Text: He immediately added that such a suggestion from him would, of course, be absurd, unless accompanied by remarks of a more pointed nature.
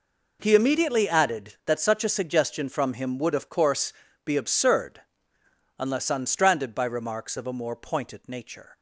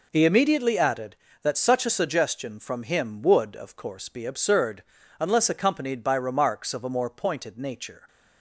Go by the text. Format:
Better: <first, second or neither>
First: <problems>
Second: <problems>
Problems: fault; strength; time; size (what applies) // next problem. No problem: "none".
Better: second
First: says "unstranded" for "accompanied"; at 6.1 s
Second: none